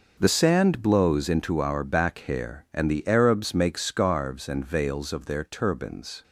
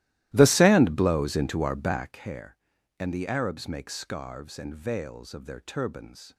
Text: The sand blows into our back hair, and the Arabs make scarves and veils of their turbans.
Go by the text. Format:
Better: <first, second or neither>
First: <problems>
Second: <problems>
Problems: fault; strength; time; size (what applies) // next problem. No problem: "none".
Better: first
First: none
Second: starts louder than the rest; strong; until 2.2 s; 15.5 dB